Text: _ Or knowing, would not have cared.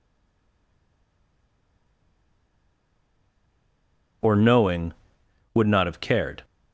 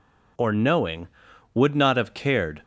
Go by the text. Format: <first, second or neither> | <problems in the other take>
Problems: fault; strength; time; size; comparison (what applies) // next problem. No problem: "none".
second | stays silent before the first word; strong; until 4.2 s; 4.2 s long